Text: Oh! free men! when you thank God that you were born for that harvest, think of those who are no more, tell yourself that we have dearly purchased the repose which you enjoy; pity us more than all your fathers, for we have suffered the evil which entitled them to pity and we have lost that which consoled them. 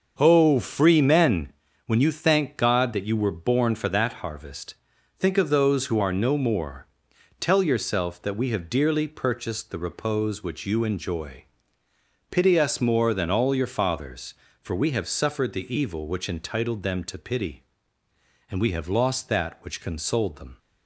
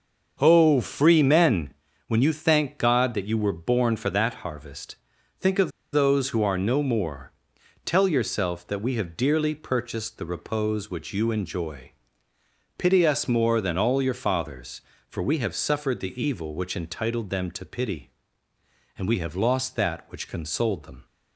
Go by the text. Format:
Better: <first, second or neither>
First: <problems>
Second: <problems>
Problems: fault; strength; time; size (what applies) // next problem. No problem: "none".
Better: first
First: starts louder than the rest; until 1.1 s; 6 dB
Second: starts louder than the rest; until 1.4 s; 6 dB // pauses between "of" and "those"; slight; at 5.7 s; 0.22 s long